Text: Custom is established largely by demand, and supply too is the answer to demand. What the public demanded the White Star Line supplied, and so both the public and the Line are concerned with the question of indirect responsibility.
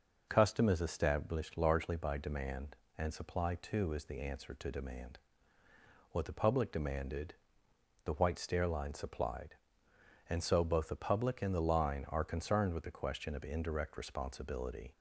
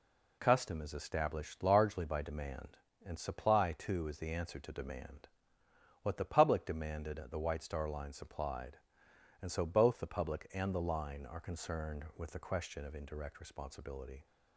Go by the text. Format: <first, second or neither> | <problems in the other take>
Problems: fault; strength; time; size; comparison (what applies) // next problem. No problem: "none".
second | pauses between "demanded" and "the"; noticeable; at 7.3 s; 0.68 s long // says "Stair" for "Star"; at 8.3 s